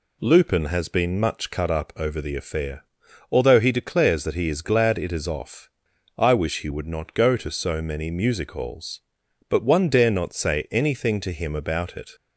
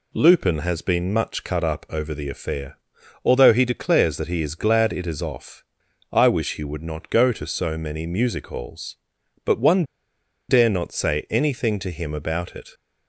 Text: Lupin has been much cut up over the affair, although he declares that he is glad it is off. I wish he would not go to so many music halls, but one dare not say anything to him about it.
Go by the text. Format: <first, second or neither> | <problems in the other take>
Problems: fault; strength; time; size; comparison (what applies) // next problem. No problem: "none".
first | pauses between "one" and "dare"; noticeable; at 9.8 s; 0.65 s long